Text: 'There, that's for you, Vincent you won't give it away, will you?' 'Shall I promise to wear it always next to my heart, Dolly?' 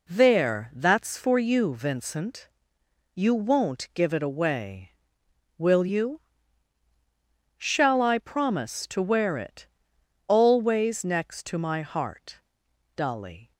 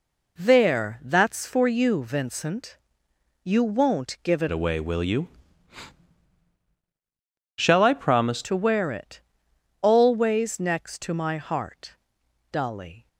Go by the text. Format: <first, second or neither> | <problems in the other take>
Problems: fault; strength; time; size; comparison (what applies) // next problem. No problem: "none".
first | pauses between "Vincent" and "you"; noticeable; at 2.7 s; 0.70 s long; noticeable in the first // changes voice from "away" to "promise"; from 4.5 to 8.4 s; 3.9 s long // pauses between "it" and "always"; noticeable; at 9.2 s; 0.60 s long; noticeable in the first